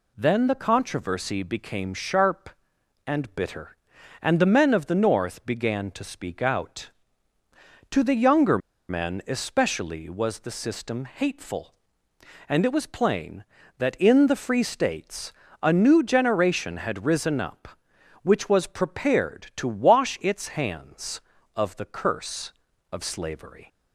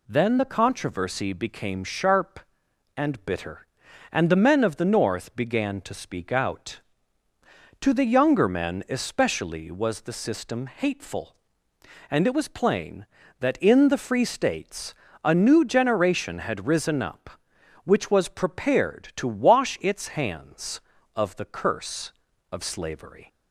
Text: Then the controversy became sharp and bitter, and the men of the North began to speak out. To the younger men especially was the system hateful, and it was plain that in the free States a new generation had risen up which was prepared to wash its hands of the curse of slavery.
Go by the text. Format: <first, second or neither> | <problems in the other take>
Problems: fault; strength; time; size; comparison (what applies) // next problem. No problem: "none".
second | pauses between "younger" and "men"; slight; at 8.5 s; 0.31 s long // pauses between "States" and "a"; slight; at 15.3 s; 0.30 s long; slight in the second